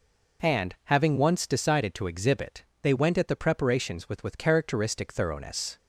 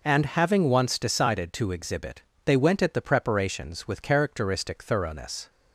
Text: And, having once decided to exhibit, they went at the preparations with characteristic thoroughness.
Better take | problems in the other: second | says "with" twice; at 4.2 s

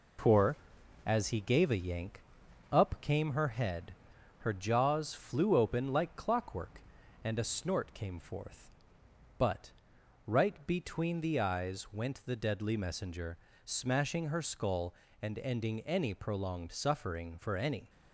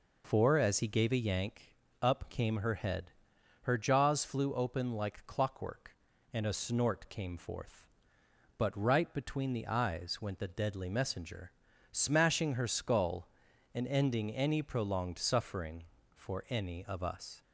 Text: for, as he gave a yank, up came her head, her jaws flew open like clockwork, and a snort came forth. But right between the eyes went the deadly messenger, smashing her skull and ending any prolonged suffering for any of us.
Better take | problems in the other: second | pauses between "But" and "right"; noticeable; at 9.7 s; 0.54 s long // stops before "of us"; at 17.8 s

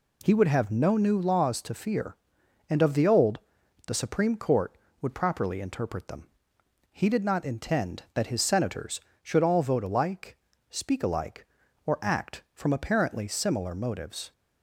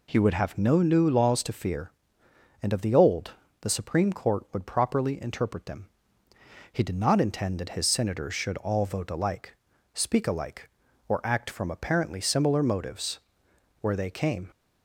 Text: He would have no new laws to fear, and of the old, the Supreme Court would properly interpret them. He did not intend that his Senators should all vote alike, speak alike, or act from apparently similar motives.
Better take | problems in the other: first | goes on to say "Where they came"; noticeable; from 13.8 s on; 0.68 s long

